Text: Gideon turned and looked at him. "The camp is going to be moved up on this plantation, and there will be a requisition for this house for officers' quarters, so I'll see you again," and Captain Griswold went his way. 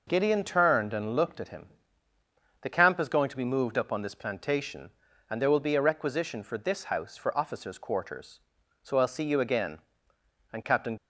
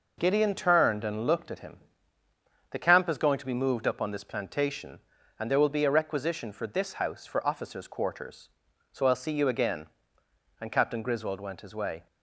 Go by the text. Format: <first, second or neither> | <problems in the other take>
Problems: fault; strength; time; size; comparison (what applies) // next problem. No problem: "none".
second | stops before "Griswold went his way"; at 10.9 s